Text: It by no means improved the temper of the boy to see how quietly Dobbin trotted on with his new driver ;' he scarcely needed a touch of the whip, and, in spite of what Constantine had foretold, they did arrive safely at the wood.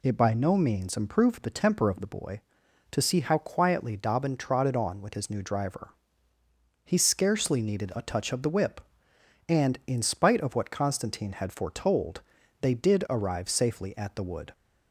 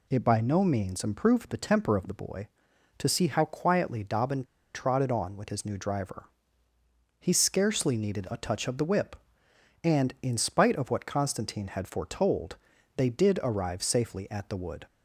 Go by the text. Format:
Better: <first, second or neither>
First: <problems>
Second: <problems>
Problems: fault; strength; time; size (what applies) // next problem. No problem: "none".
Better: first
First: none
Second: pauses between "Dobbin" and "trotted"; slight; at 4.4 s; 0.30 s long